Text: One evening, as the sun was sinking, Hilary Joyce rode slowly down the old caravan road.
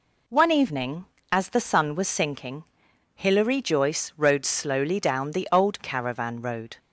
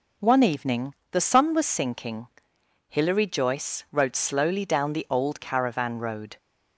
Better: first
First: none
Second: skips "as"; at 1.0 s

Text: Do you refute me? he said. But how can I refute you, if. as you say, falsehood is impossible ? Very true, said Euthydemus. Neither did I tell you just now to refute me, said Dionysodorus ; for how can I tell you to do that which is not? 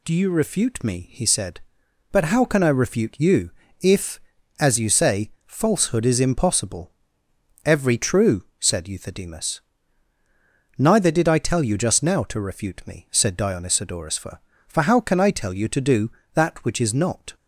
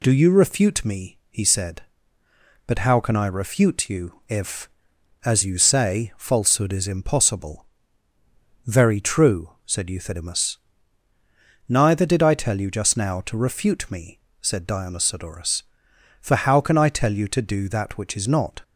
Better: second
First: says "Every" for "Very"; at 7.6 s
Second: none

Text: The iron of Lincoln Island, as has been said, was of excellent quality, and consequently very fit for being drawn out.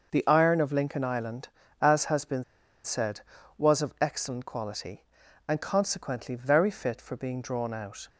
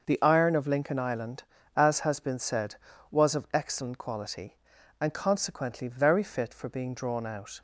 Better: second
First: starts louder than the rest; noticeable; until 1.1 s; 6 dB // pauses between "been" and "said"; at 2.4 s; 0.40 s long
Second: starts louder than the rest; noticeable; until 1.1 s; 6 dB

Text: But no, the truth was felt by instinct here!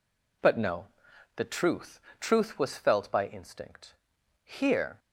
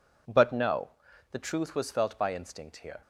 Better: second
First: says "truth" twice; at 2.2 s // pauses between "instinct" and "here"; noticeable; at 3.9 s; 0.50 s long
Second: none

